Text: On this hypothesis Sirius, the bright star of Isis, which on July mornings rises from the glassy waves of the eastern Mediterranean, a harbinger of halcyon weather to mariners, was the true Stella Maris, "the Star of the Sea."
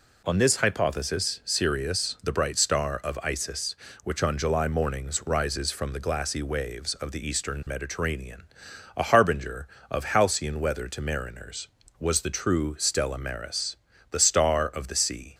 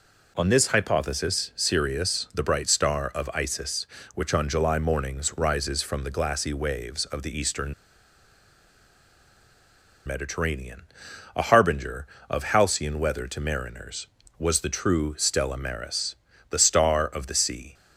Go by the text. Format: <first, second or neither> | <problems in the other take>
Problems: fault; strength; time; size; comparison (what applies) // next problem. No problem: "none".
first | pauses between "eastern" and "Mediterranean"; strong; at 7.7 s; 2.3 s long